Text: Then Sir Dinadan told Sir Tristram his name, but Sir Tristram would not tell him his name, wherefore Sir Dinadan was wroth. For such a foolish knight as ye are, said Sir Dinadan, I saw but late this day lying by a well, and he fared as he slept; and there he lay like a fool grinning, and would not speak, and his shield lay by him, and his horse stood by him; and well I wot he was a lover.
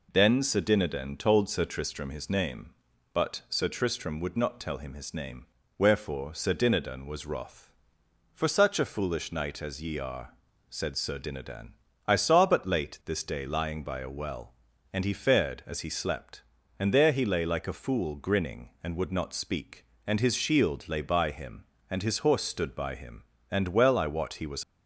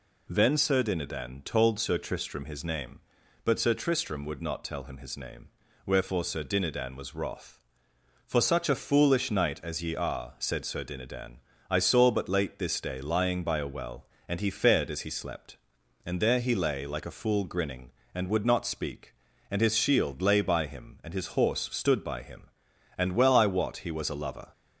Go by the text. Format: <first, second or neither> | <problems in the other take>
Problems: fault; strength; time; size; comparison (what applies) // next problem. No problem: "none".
second | stops before "a lover"; at 24.6 s